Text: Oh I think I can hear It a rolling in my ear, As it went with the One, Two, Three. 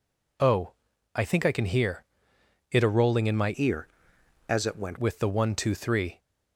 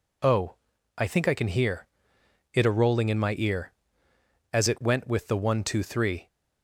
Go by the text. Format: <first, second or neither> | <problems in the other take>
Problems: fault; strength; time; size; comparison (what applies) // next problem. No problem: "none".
second | pauses between "Oh" and "I"; at 0.7 s; 0.42 s long; also in the second // pauses between "hear" and "It"; noticeable; at 2.0 s; 0.68 s long; noticeable in the second // changes voice from "ear" to "went"; from 3.5 to 4.9 s; 1.4 s long